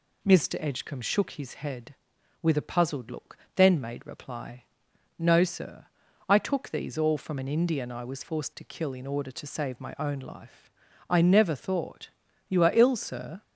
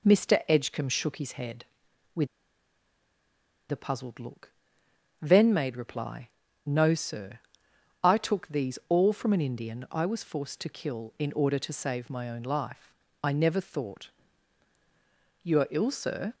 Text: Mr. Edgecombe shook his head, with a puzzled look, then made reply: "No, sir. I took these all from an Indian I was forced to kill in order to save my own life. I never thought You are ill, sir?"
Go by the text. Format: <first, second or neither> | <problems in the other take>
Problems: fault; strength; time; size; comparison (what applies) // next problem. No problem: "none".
first | pauses between "with" and "a"; strong; at 2.2 s; 1.4 s long // pauses between "thought" and "You"; strong; at 14.0 s; 1.3 s long; also in the first